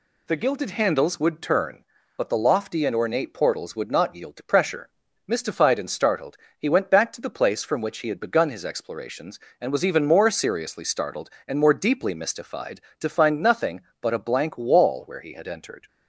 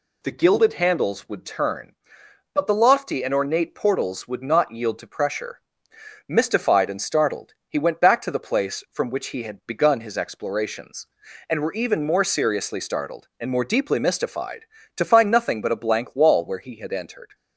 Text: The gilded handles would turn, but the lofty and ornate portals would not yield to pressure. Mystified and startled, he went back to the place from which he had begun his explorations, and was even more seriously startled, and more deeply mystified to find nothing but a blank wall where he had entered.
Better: first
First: none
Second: says "were" for "was"; at 11.6 s

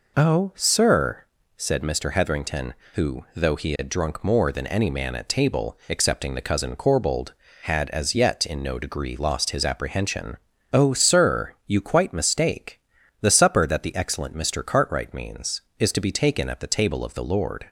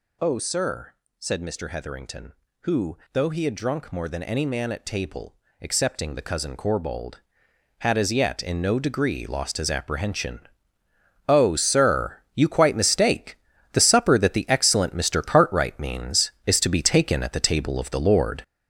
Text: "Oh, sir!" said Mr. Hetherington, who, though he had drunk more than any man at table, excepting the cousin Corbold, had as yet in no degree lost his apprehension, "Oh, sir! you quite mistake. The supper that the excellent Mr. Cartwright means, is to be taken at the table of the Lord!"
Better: first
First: none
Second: gets louder; strong; throughout; 7.5 dB

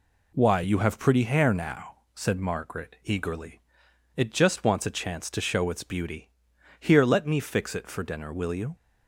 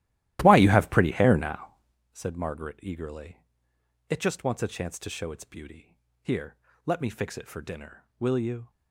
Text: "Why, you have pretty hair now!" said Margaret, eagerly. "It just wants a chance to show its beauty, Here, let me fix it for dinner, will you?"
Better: first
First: none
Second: starts louder than the rest; strong; until 2.0 s; 15 dB

